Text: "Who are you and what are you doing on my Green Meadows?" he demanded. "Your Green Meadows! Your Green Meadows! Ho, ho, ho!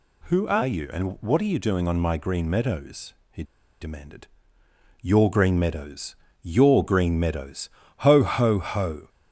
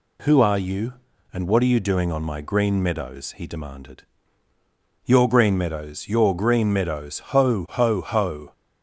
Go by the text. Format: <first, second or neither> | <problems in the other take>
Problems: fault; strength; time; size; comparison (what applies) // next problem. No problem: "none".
second | pauses between "he" and "demanded"; at 3.4 s; 0.37 s long